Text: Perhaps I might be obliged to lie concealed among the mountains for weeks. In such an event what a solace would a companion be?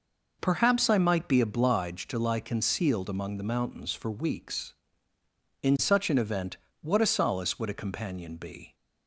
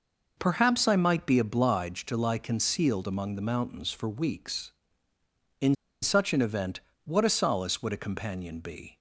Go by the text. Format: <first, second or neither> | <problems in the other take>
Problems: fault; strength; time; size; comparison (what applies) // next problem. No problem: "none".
first | pauses between "In" and "such"; slight; at 5.7 s; 0.27 s long // pauses between "event" and "what"; slight; at 6.7 s; 0.24 s long; slight in the first